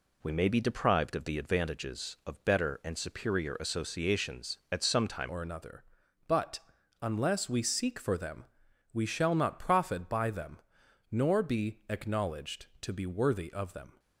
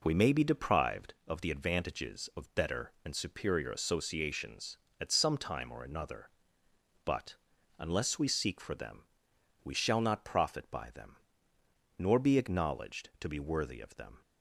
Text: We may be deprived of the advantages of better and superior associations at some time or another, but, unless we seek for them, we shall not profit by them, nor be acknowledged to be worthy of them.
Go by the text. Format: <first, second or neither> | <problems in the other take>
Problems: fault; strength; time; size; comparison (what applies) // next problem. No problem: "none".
second | changes voice at "or"; from 5.2 s on; 8.7 s long